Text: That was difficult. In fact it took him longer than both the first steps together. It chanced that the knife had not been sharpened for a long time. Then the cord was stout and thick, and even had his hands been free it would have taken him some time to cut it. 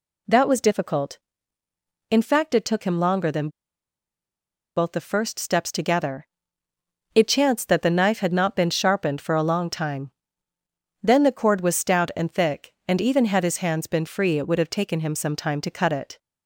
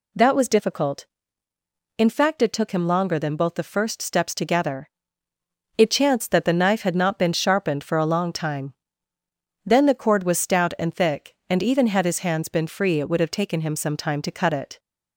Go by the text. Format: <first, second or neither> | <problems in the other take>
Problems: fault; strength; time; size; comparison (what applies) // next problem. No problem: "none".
second | pauses between "than" and "both"; strong; at 3.4 s; 1.2 s long